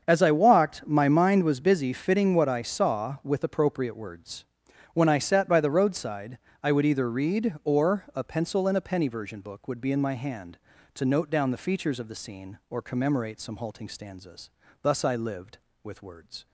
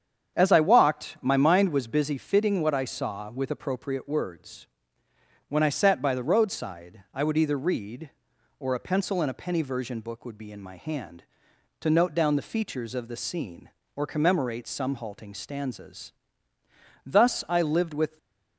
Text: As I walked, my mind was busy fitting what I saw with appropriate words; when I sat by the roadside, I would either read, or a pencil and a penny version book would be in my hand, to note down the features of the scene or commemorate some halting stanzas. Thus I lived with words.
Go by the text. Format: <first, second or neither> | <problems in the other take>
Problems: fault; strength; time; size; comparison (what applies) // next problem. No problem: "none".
first | starts louder than the rest; strong; until 1.4 s; 8 dB; also in the first // stays silent after the last word; slight; from 18.0 s on; 0.5 s long // stops before "words"; at 18.1 s